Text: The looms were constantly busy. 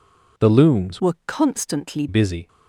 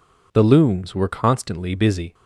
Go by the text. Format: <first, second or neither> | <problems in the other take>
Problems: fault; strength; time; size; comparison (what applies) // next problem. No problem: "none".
second | changes voice from "were" to "constantly"; from 1.0 to 2.0 s; 1.0 s long